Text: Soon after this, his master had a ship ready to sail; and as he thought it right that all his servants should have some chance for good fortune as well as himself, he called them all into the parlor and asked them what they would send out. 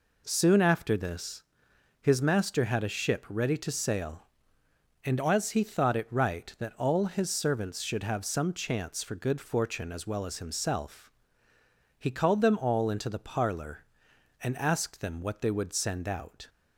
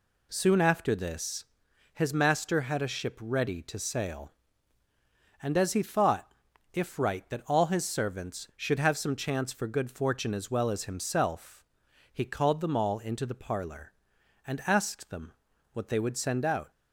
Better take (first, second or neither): first